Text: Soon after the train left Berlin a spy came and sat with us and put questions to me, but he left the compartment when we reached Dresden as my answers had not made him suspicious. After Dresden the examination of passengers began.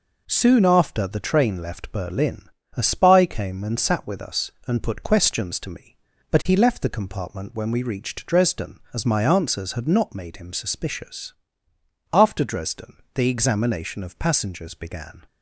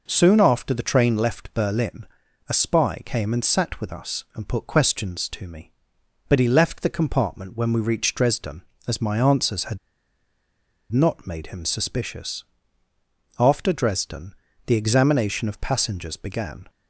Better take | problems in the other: first | pauses between "Berlin" and "a"; at 2.0 s; 0.42 s long; slight in the first // pauses between "had" and "not"; at 9.7 s; 1.1 s long // pauses between "Dresden" and "the"; slight; at 14.3 s; 0.34 s long; slight in the first

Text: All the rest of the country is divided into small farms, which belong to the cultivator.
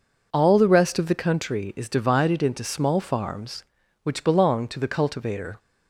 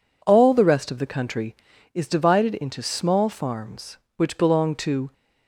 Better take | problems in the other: first | stops before "the cultivator"; at 5.1 s

